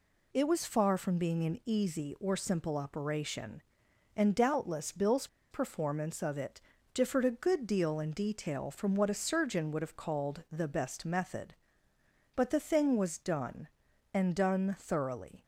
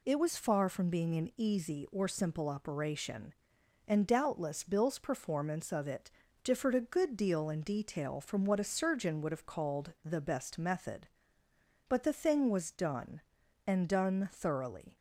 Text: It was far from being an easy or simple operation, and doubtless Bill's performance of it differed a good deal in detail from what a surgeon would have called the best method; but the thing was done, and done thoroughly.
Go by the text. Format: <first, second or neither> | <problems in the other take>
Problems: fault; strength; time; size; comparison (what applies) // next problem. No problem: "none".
second | pauses between "Bill's" and "performance"; slight; at 5.2 s; 0.24 s long // pauses between "it" and "differed"; slight; at 6.6 s; 0.32 s long; slight in the second